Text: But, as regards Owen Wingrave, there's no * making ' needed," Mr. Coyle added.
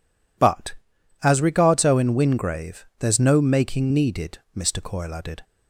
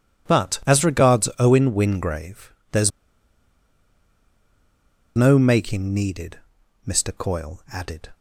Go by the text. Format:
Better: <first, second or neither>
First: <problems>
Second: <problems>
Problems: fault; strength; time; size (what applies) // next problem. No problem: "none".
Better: first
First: none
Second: pauses between "there's" and "no"; strong; at 2.9 s; 2.2 s long